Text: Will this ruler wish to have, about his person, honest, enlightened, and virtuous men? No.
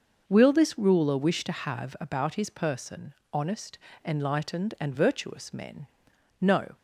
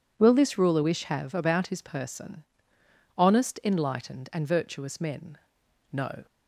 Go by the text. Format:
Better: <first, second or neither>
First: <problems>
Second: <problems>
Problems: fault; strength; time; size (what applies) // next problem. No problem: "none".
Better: first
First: none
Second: skips "to"; at 1.0 s